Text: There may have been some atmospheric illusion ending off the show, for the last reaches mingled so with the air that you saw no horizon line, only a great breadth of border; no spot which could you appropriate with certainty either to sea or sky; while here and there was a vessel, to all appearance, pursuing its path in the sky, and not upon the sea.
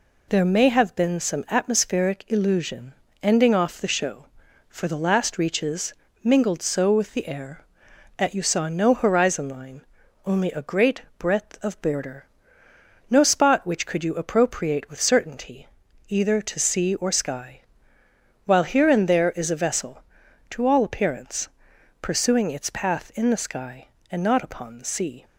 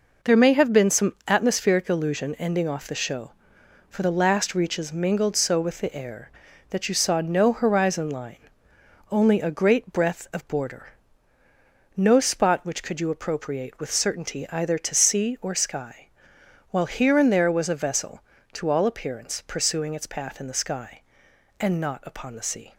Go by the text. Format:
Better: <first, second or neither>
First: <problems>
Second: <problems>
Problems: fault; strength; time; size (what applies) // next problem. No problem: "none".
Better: second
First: pauses between "illusion" and "ending"; slight; at 2.9 s; 0.30 s long // pauses between "reaches" and "mingled"; slight; at 5.9 s; 0.28 s long // pauses between "great" and "breadth"; slight; at 11.0 s; 0.16 s long // pauses between "certainty" and "either"; at 15.6 s; 0.44 s long // says "is" for "was"; at 19.3 s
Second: none